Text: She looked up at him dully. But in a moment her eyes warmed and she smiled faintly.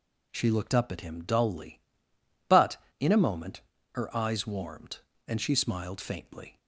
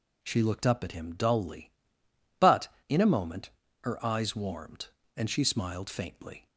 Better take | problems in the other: neither | pauses between "moment" and "her"; slight; the same in both

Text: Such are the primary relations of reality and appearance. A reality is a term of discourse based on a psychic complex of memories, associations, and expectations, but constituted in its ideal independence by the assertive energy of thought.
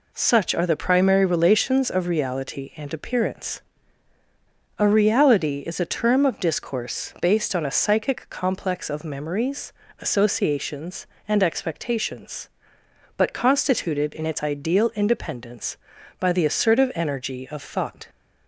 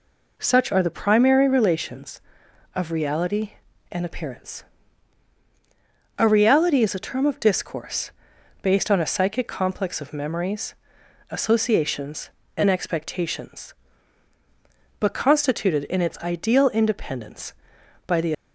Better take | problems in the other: first | pauses between "discourse" and "based"; noticeable; at 8.1 s; 0.52 s long // stops before "assertive energy of thought"; at 18.3 s

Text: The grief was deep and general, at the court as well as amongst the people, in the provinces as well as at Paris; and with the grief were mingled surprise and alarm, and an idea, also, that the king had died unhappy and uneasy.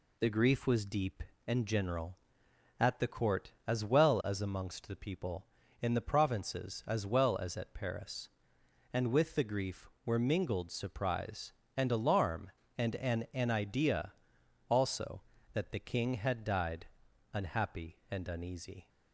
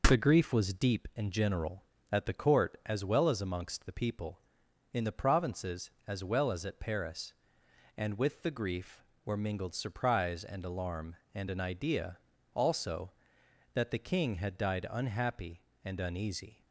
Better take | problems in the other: second | says "an" twice; at 13.3 s // pauses between "died" and "unhappy"; noticeable; at 16.8 s; 0.46 s long

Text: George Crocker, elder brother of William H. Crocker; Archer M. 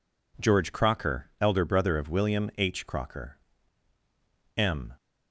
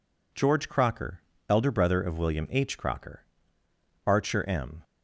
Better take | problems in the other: second | skips "Archer"; at 3.9 s

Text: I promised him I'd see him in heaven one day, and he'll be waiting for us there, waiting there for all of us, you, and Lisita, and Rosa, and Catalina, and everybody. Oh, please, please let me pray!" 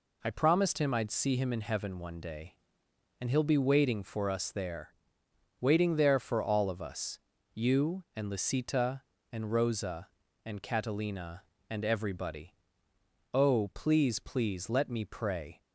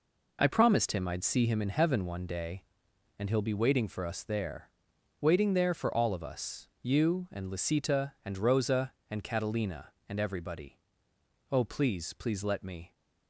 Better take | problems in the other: first | stops before "pray"; at 12.9 s

